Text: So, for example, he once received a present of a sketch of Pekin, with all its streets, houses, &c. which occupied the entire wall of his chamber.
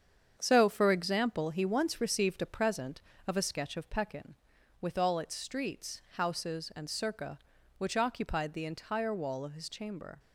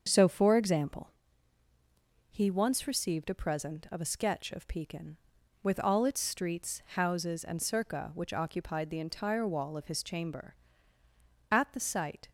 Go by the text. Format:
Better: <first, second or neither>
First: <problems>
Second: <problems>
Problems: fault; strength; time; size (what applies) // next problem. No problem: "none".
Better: first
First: starts louder than the rest; strong; until 1.3 s; 7.5 dB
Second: starts louder than the rest; until 1.0 s; 6.5 dB // goes on to say "At the sight"; noticeable; from 11.5 s on; 0.78 s long